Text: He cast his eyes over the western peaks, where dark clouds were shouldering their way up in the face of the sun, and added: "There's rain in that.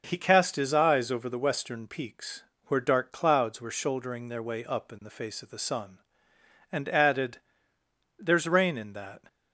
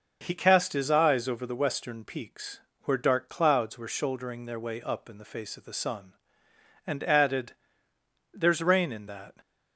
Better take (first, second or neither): neither